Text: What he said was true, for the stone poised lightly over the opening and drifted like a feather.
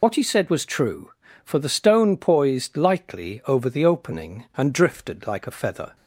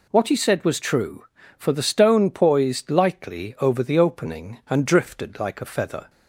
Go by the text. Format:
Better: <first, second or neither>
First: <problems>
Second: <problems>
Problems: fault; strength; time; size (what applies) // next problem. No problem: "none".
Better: second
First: loses the start of "What"; at 0.0 s; 60 ms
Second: none